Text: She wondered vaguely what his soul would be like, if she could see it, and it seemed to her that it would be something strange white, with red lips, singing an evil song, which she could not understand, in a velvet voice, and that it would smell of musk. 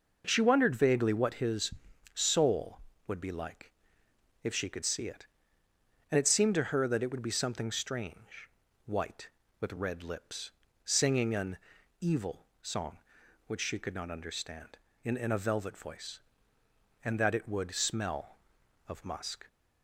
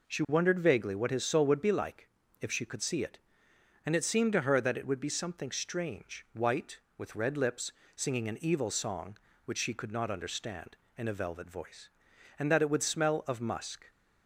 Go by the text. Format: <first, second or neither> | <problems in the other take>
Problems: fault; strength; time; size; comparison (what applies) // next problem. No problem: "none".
second | pauses between "his" and "soul"; at 1.7 s; 0.42 s long // pauses between "strange" and "white"; slight; at 8.4 s; 0.36 s long // pauses between "an" and "evil"; noticeable; at 11.5 s; 0.46 s long // says "in" twice; at 15.1 s